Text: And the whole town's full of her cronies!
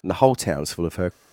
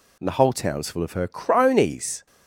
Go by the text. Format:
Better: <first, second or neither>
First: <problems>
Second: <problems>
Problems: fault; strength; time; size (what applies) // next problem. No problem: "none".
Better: second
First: stops before "cronies"; at 1.1 s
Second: none